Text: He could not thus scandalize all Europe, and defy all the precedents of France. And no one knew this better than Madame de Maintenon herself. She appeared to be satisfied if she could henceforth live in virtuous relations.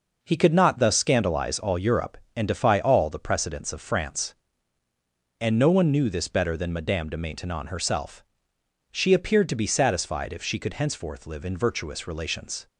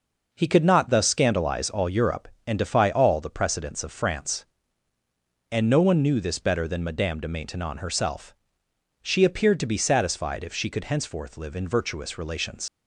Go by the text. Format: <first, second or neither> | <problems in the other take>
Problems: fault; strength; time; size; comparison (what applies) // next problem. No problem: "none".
first | leaves "relations" unfinished; at 12.6 s; 95 ms